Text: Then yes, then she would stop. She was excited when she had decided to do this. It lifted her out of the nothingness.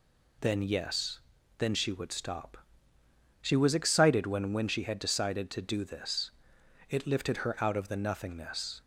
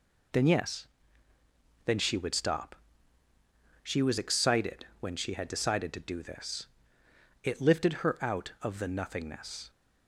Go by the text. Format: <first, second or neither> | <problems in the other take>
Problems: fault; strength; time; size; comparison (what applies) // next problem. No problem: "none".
second | says "when" twice; at 4.5 s